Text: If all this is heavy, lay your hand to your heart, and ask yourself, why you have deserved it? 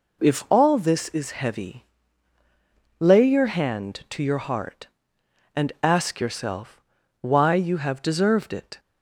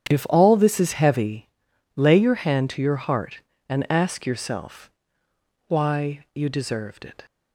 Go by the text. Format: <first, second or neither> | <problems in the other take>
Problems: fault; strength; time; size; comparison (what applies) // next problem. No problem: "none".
first | starts louder than the rest; strong; until 1.1 s; 9 dB // skips "have"; at 6.4 s